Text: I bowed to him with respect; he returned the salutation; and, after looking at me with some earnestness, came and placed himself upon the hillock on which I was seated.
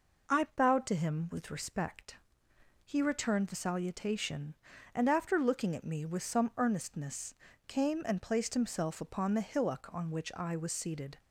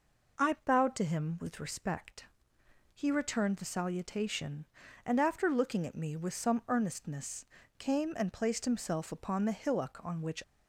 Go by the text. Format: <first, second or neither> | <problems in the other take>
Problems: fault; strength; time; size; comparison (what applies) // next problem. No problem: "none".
first | stops before "I was seated"; at 10.4 s